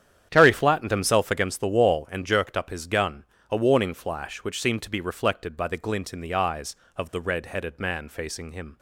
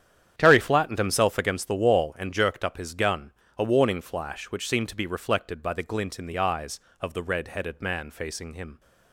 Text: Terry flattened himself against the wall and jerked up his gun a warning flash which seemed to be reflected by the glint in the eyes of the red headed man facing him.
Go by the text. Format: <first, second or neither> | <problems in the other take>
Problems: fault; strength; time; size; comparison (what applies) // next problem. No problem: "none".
neither | starts louder than the rest; strong; the same in both // pauses between "gun" and "a"; slight; the same in both